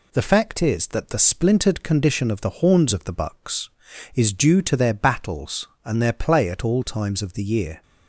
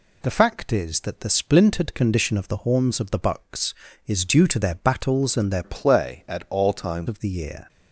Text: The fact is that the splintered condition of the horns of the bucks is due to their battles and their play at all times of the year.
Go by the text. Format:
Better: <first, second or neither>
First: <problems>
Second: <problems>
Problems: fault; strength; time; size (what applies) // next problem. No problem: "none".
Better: first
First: none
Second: changes voice from "play" to "times"; from 5.6 to 7.0 s; 1.4 s long